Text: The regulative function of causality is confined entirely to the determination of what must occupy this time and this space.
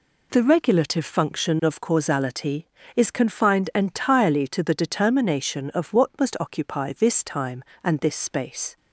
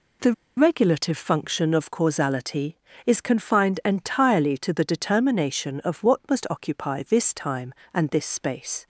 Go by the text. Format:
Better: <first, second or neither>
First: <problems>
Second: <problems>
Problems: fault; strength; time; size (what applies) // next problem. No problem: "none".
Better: first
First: none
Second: pauses between "The" and "regulative"; slight; at 0.3 s; 0.23 s long